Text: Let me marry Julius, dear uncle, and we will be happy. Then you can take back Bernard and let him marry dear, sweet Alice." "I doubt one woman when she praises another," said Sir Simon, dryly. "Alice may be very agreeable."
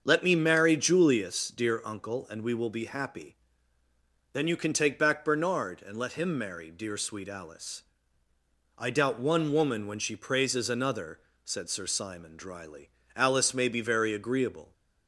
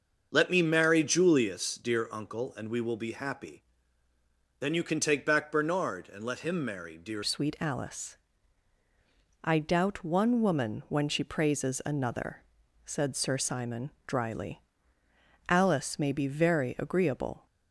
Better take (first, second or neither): first